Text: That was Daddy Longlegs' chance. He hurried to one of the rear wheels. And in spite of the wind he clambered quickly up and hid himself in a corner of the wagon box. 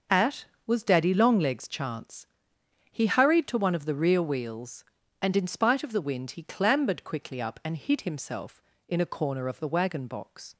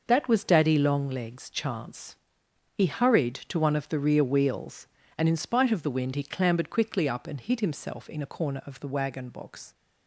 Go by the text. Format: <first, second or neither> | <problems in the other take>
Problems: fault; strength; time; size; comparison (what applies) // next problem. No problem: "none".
second | starts louder than the rest; until 1.3 s; 6 dB; noticeable in the second // says "At" for "That"; at 0.1 s